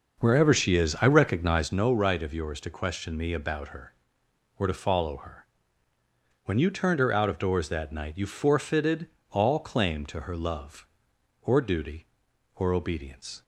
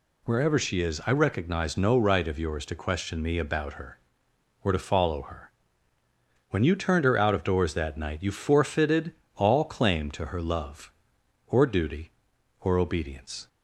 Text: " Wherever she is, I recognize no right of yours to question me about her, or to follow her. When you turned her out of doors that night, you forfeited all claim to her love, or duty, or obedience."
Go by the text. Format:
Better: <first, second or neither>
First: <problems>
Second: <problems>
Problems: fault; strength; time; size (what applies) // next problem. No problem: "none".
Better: second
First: starts louder than the rest; noticeable; until 1.7 s; 6 dB // pauses between "forfeited" and "all"; slight; at 9.0 s; 0.24 s long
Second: pauses between "forfeited" and "all"; slight; at 9.1 s; 0.24 s long